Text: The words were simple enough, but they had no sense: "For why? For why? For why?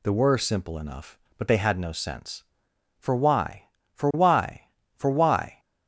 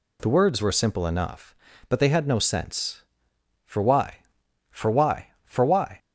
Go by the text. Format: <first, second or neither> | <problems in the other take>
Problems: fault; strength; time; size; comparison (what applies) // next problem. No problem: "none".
second | skips "words"; at 0.1 s